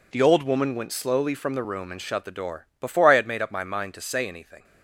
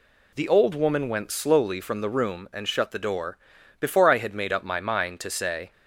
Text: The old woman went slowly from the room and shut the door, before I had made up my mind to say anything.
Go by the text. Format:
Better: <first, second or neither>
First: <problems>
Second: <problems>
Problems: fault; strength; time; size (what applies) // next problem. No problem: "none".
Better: first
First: none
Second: stops before "anything"; at 5.7 s